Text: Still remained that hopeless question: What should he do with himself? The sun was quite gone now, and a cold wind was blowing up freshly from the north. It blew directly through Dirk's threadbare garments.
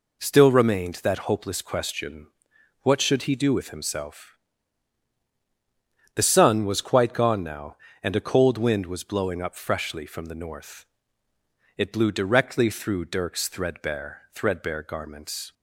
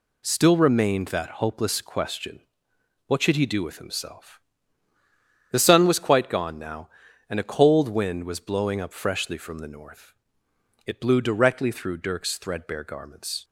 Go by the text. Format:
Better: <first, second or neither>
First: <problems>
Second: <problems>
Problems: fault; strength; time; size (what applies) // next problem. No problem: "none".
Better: second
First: says "threadbare" twice; at 14.3 s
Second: none